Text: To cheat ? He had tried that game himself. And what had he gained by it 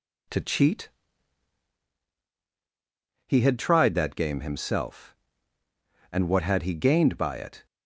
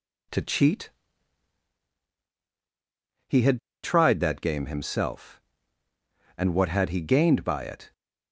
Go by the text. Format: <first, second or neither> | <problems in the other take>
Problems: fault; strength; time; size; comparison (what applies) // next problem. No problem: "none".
first | pauses between "had" and "tried"; slight; at 3.5 s; 0.24 s long